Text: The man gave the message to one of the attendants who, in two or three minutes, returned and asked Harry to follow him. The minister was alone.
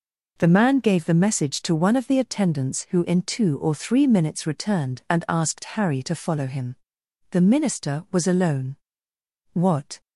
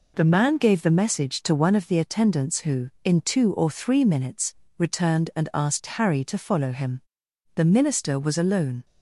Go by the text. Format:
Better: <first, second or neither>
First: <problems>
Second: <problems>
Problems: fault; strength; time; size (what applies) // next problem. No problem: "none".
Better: second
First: goes on to say "What"; slight; from 9.5 s on; 0.48 s long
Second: none